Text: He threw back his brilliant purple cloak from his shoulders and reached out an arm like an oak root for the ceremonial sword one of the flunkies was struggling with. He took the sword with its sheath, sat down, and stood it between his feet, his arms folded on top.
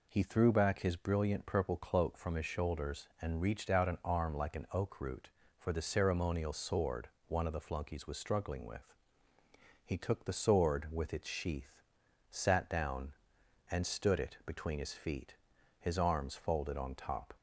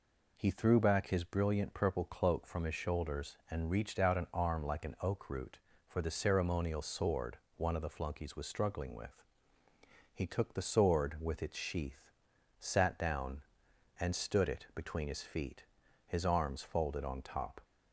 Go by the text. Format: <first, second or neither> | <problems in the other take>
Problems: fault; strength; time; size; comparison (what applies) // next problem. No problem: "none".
neither | pauses between "sword" and "one"; slight; the same in both